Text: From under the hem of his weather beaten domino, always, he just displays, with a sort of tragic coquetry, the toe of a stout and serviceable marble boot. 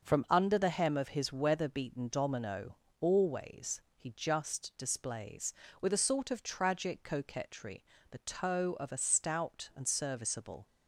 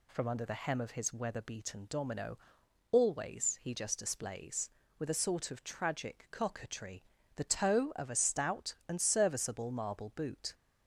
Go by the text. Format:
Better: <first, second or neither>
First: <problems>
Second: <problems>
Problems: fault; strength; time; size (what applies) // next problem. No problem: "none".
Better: second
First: starts louder than the rest; until 1.0 s; 6.5 dB // stops before "marble boot"; at 10.6 s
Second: none